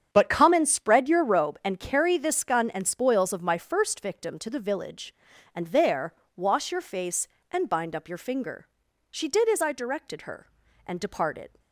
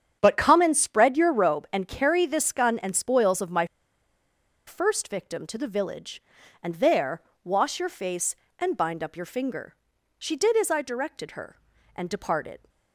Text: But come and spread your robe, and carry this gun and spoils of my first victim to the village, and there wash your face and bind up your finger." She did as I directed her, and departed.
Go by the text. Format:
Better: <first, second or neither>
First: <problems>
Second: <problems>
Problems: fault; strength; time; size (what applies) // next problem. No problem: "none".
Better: first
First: starts louder than the rest; strong; until 1.1 s; 8.5 dB // pauses between "there" and "wash"; slight; at 6.1 s; 0.22 s long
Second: starts louder than the rest; strong; until 1.2 s; 8.5 dB // pauses between "my" and "first"; at 3.6 s; 1.0 s long // pauses between "there" and "wash"; slight; at 7.2 s; 0.22 s long